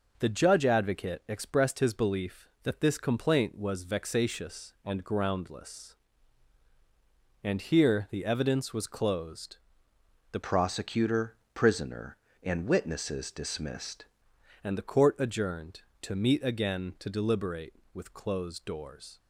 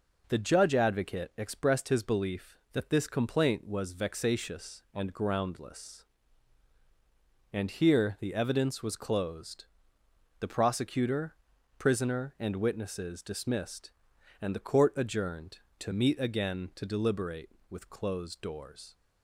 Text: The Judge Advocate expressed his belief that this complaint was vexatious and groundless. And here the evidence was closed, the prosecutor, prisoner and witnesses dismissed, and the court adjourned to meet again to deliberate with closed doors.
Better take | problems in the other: second | changes voice from "prosecutor" to "dismissed"; from 10.4 to 14.0 s; 3.6 s long

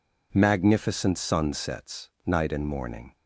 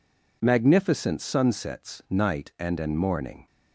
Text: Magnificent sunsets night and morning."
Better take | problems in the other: first | says "and" twice; at 2.8 s

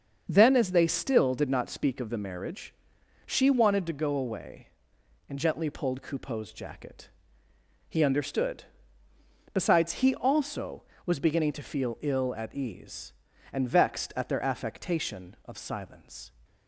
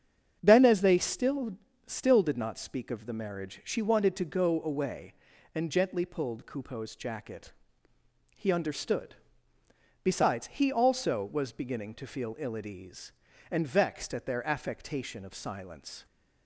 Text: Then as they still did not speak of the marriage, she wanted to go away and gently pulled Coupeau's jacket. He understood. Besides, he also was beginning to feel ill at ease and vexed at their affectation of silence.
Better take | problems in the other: first | starts louder than the rest; strong; until 1.4 s; 7.5 dB; also in the first // says "still" twice; at 1.8 s

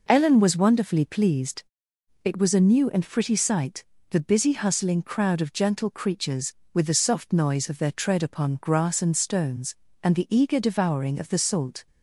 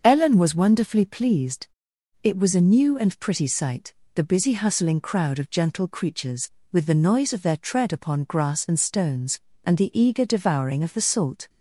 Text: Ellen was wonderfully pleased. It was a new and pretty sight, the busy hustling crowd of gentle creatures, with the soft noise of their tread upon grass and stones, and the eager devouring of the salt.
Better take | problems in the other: first | starts louder than the rest; until 1.0 s; 6.5 dB // skips "soft"; at 6.9 s

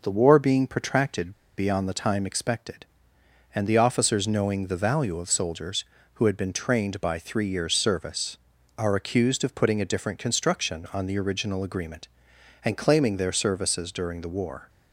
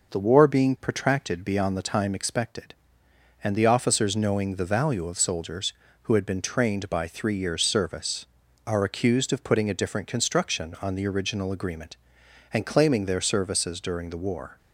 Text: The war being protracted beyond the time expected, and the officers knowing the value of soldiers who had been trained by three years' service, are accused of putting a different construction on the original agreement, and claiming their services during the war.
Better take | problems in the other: second | pauses between "protracted" and "beyond"; slight; at 1.3 s; 0.26 s long

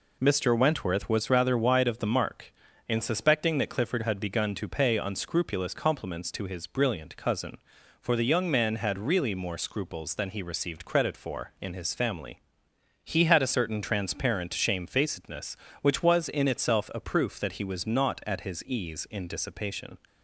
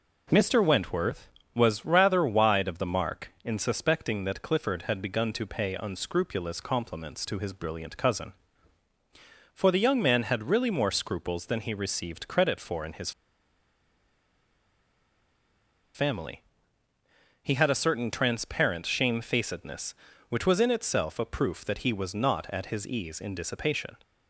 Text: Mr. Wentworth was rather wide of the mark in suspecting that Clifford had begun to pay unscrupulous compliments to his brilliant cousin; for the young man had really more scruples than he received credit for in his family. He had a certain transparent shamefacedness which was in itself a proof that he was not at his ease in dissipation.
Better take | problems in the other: first | pauses between "his" and "family"; strong; at 13.1 s; 2.8 s long

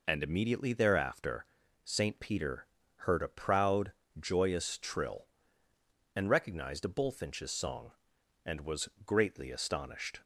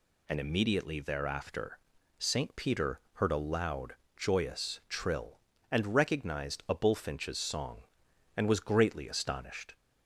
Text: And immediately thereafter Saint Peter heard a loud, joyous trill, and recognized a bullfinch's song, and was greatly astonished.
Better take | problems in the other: second | pauses between "thereafter" and "Saint"; at 1.4 s; 0.40 s long; also in the second // pauses between "Peter" and "heard"; slight; at 2.6 s; 0.30 s long // says "proud" for "loud"; at 3.2 s // pauses between "was" and "greatly"; slight; at 8.8 s; 0.16 s long

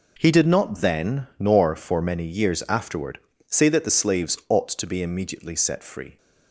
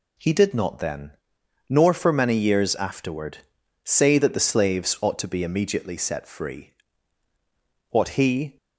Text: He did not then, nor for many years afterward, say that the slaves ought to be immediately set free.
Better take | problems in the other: first | goes on to say "What he"; noticeable; from 7.8 s on; 0.66 s long

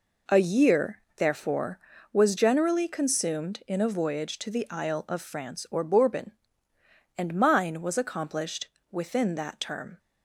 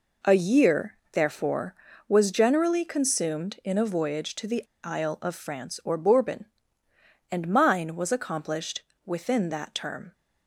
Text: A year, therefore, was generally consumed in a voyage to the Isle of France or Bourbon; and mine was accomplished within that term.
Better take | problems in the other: first | pauses between "the" and "Isle"; slight; at 4.6 s; 0.20 s long // pauses between "accomplished" and "within"; slight; at 8.8 s; 0.22 s long; slight in the first

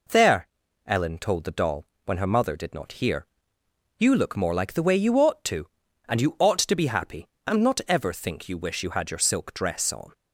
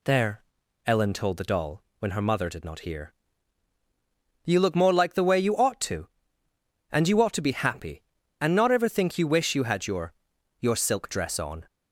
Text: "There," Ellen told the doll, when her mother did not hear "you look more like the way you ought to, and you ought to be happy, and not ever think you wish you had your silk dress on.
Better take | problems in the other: first | pauses between "hear" and "you"; strong; at 3.1 s; 1.3 s long; noticeable in the first // says "your" twice; at 10.5 s

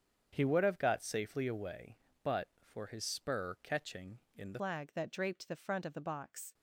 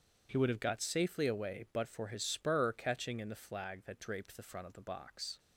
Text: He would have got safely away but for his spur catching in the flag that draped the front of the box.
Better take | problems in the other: second | starts louder than the rest; strong; until 1.3 s; 7.5 dB // changes voice at "flag"; from 4.5 s on; 2.0 s long

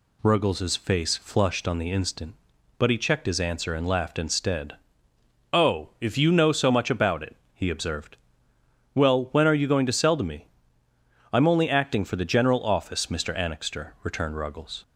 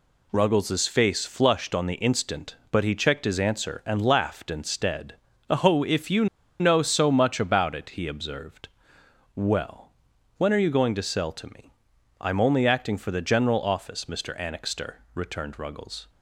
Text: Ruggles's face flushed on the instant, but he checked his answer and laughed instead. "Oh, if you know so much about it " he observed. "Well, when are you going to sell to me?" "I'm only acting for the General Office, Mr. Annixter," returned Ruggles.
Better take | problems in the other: first | pauses between "you" and "know"; slight; at 6.2 s; 0.34 s long

